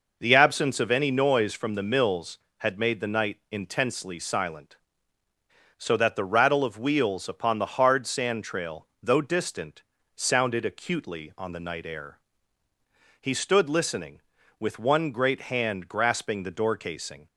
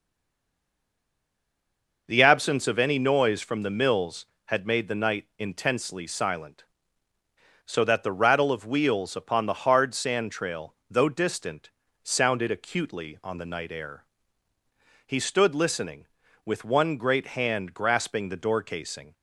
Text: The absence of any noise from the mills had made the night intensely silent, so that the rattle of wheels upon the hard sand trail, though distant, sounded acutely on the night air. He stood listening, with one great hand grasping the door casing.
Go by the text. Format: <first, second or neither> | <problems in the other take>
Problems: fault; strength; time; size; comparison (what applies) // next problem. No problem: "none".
first | stays silent before the first word; noticeable; until 2.0 s; 2.0 s long